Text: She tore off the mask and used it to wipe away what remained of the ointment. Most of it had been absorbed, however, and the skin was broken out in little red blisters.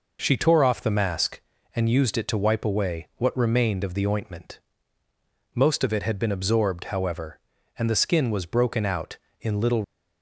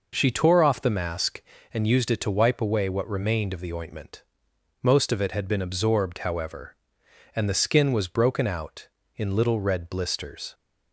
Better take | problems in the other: second | stops before "red blisters"; at 9.8 s

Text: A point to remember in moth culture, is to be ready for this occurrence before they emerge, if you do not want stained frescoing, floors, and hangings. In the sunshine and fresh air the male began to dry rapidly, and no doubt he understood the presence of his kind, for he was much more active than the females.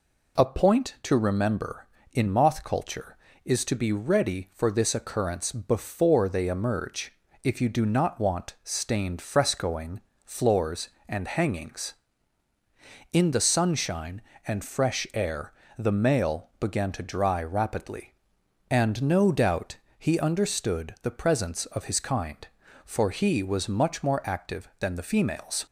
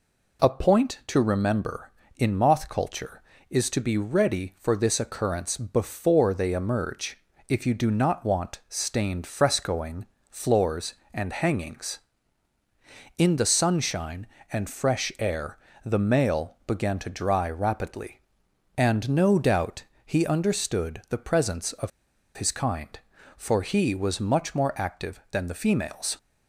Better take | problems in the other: first | pauses between "air" and "the"; slight; at 15.5 s; 0.26 s long; slight in the first // pauses between "doubt" and "he"; slight; at 19.8 s; 0.20 s long; slight in the first // pauses between "of" and "his"; noticeable; at 21.9 s; 0.47 s long

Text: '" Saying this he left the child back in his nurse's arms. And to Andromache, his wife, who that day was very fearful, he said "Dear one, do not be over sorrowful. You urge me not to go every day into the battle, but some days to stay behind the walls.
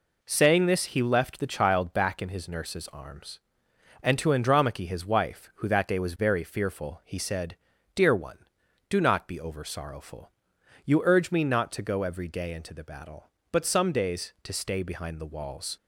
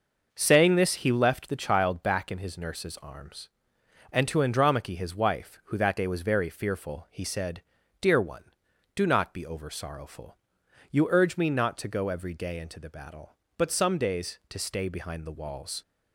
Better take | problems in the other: first | starts louder than the rest; noticeable; until 1.5 s; 6 dB // pauses between "said" and "Dear"; at 7.6 s; 0.38 s long; also in the first

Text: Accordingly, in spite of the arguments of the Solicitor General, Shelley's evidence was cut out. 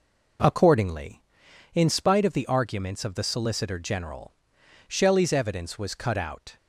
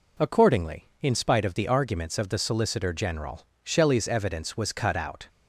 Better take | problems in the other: neither | none

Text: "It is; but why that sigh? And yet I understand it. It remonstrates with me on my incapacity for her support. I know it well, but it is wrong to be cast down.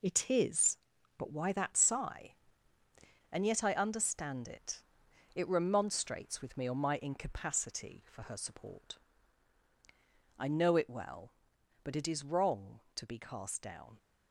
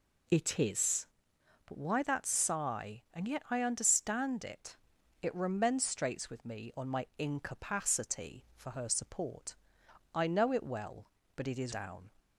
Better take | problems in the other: first | skips "wrong to be cast"; at 11.7 s

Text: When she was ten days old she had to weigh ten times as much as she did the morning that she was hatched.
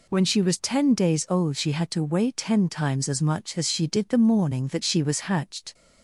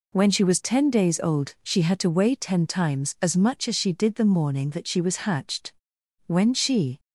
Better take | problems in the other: first | goes on to say "When she"; noticeable; from 6.2 s on; 0.72 s long

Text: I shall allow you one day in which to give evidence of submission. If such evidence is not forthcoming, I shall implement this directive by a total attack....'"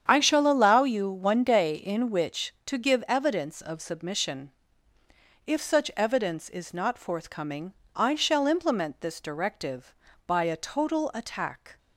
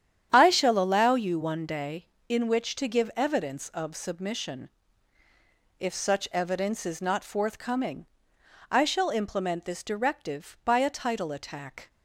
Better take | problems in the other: first | starts louder than the rest; strong; until 1.3 s; 9.5 dB; strong in the first // says "title" for "total"; at 10.9 s

